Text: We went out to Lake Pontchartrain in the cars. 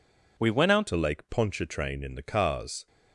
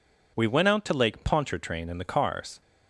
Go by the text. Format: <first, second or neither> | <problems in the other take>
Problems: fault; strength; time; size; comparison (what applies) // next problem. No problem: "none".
second | changes voice at "to"; from 0.8 s on; 2.0 s long